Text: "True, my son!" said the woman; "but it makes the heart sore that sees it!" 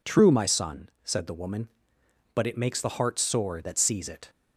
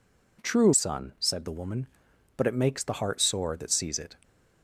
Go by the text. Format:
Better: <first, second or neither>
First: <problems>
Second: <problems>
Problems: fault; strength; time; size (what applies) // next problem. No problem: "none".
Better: first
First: none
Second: skips "my"; at 0.7 s